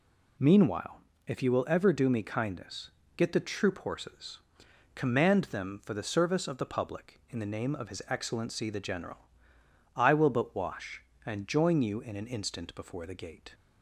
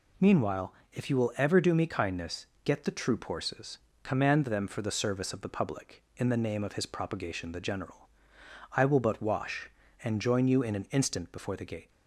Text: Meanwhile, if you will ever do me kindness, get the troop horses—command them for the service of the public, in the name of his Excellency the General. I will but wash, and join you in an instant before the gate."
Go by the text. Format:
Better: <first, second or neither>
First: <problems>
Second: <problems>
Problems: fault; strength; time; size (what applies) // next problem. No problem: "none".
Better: first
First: none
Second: says "Propagation" for "Excellency"; at 6.8 s